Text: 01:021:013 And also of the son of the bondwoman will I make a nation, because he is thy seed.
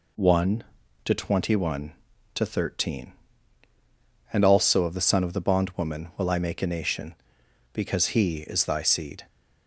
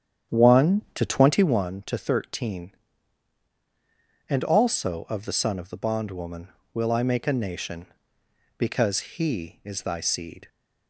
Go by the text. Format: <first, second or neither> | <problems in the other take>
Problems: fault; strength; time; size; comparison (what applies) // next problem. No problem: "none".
first | starts louder than the rest; strong; until 1.6 s; 9 dB